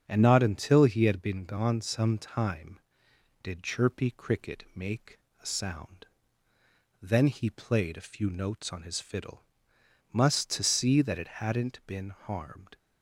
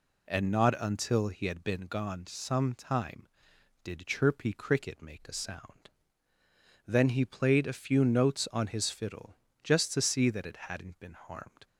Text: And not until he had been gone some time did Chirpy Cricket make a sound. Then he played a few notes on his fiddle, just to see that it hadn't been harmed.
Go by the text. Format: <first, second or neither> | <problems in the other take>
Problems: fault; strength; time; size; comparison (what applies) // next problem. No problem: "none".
second | starts louder than the rest; strong; until 1.0 s; 7.5 dB // pauses between "make" and "a"; slight; at 5.1 s; 0.22 s long // says "must" for "just"; at 10.1 s